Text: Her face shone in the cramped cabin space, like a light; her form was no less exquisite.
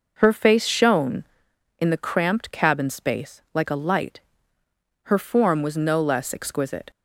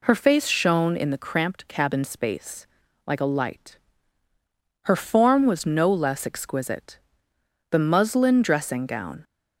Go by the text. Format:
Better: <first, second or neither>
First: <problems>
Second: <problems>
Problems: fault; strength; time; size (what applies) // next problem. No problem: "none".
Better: first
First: none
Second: goes on to say "The muslin dressing gown"; from 7.7 s on; 1.5 s long